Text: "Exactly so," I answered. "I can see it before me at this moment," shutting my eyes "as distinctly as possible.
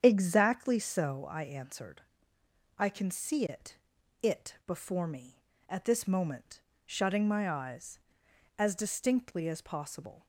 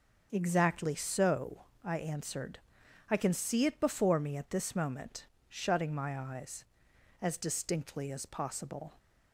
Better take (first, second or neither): second